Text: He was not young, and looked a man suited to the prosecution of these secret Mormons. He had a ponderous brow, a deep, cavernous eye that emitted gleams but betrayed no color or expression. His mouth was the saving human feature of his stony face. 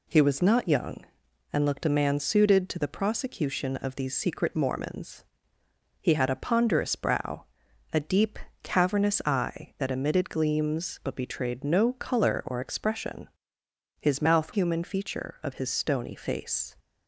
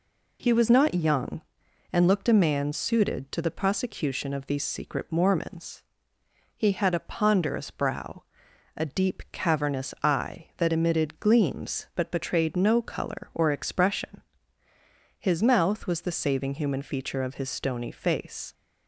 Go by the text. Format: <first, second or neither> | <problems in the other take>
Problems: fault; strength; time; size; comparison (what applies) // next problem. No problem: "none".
second | skips "was the saving"; at 14.5 s